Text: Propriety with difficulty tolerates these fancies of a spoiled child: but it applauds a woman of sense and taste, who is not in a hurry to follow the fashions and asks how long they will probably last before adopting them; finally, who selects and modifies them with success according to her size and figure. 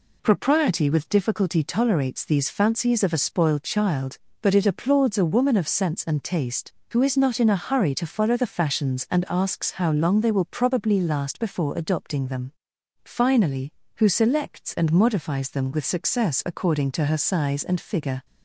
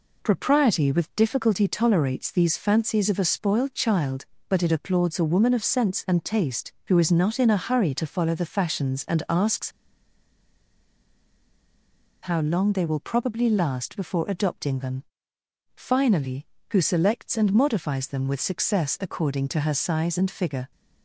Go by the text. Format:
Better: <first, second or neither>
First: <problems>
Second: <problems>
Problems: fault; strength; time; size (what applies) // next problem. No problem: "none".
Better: first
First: none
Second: pauses between "asks" and "how"; strong; at 9.6 s; 2.5 s long